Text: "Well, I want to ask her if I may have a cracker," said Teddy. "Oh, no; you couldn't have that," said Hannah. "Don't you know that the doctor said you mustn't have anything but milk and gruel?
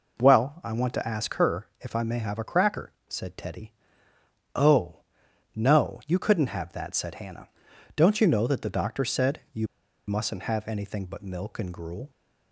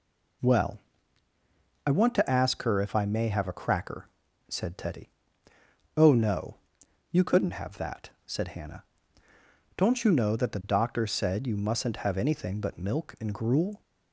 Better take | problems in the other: second | pauses between "you" and "mustn't"; at 9.6 s; 0.41 s long

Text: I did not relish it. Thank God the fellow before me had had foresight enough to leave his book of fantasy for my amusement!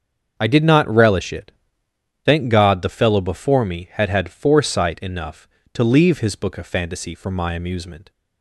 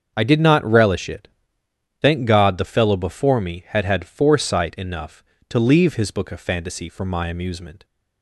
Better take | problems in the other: neither | starts louder than the rest; the same in both

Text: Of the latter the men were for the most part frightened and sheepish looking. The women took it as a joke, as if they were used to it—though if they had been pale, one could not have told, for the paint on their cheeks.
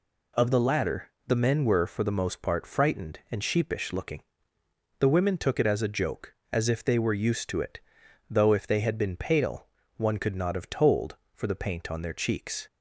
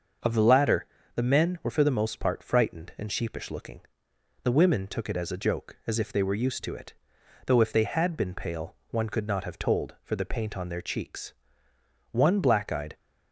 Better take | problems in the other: first | starts louder than the rest; until 1.5 s; 6.5 dB // pauses between "latter" and "the"; slight; at 0.8 s; 0.28 s long; slight in the first // goes on to say "One black eyed"; noticeable; from 12.1 s on; 0.84 s long

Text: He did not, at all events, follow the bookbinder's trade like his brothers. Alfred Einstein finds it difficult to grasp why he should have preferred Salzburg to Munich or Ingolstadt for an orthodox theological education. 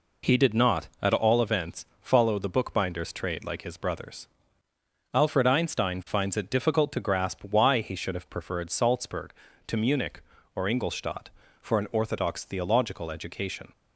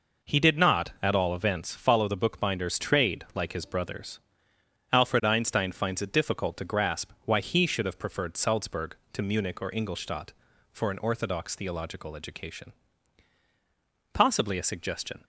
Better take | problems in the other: first | goes on to say "Possibly a suggestion"; noticeable; from 14.1 s on; 1.1 s long

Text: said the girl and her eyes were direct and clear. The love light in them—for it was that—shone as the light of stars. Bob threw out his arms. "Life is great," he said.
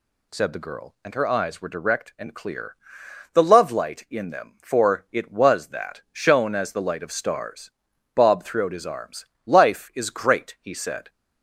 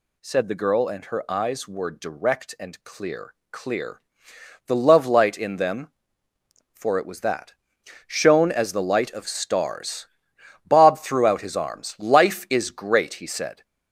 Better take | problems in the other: first | says "clear" twice; at 3.5 s

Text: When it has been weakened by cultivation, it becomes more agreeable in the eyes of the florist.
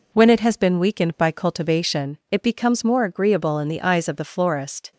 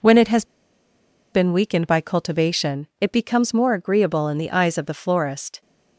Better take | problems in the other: first | pauses between "has" and "been"; noticeable; at 0.4 s; 0.86 s long

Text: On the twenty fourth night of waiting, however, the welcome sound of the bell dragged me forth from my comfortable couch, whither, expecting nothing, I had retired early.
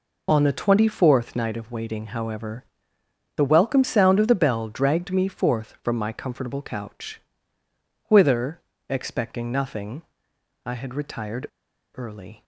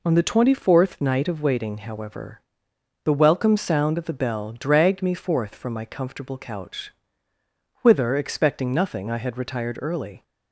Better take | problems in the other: second | pauses between "retired" and "early"; at 11.4 s; 0.45 s long

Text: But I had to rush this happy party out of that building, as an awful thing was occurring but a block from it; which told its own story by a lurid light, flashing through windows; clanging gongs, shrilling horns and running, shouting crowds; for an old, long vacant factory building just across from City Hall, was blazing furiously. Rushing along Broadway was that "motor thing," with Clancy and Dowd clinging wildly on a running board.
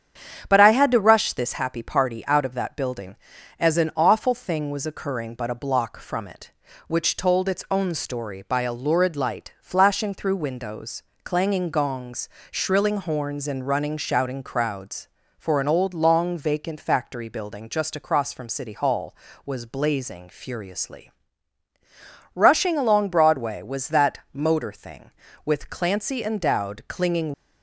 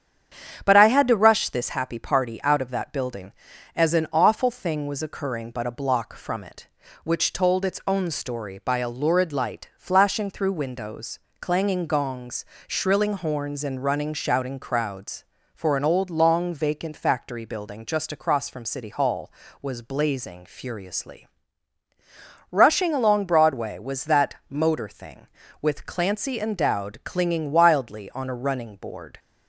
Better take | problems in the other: second | starts louder than the rest; strong; until 1.5 s; 8.5 dB; strong in the second // stops before "wildly on a running board"; at 27.3 s

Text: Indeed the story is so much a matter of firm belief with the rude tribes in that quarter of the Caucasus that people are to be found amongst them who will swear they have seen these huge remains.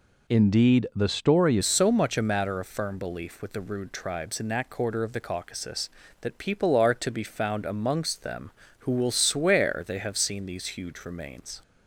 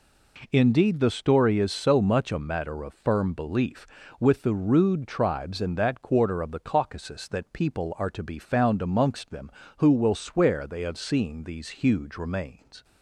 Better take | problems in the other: second | changes voice at "is"; from 1.6 s on; 10.0 s long

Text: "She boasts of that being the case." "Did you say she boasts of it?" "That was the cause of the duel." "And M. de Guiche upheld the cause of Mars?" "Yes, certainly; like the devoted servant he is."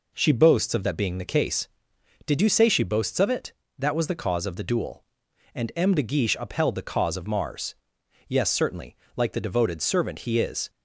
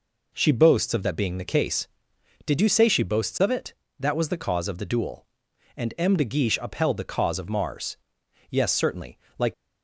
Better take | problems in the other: first | stops before "the devoted servant he is"; at 9.5 s

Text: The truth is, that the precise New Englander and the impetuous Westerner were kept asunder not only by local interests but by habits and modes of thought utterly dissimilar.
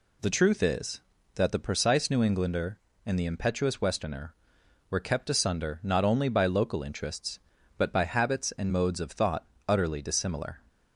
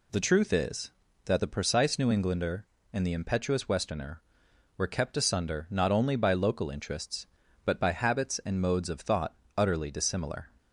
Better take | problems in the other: neither | pauses between "thought" and "utterly"; slight; the same in both

